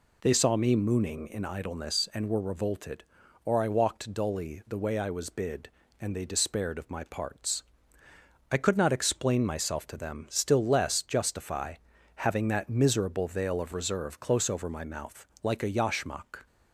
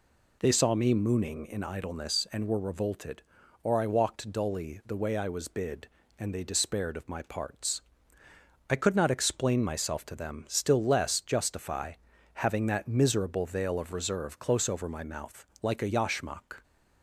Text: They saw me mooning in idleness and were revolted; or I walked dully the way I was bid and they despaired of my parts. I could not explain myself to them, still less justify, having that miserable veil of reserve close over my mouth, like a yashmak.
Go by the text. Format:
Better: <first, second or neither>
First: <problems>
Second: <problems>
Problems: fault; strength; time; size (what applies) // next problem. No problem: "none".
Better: neither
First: none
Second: none